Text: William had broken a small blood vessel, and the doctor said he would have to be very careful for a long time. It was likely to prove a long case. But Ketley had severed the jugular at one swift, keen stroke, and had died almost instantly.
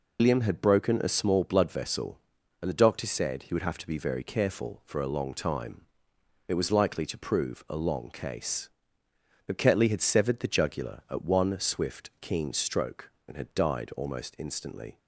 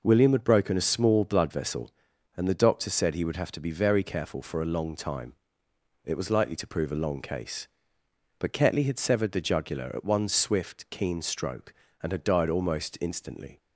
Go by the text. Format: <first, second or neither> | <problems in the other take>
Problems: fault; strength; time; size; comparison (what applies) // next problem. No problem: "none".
second | loses the start of "William"; at 0.1 s; 115 ms